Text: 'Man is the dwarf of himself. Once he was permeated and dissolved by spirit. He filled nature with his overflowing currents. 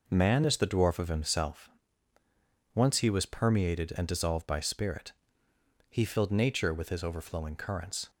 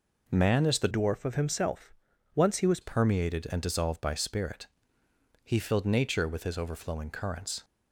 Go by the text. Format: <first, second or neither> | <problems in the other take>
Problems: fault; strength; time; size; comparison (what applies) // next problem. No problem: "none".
first | changes voice from "dwarf" to "was"; from 0.9 to 2.7 s; 1.8 s long